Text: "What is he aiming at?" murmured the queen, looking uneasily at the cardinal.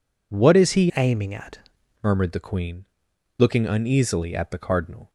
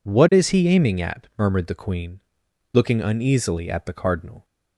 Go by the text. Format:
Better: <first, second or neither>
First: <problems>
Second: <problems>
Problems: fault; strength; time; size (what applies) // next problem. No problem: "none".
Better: second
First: changes voice from "aiming" to "at"; from 0.9 to 1.5 s; 0.6 s long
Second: none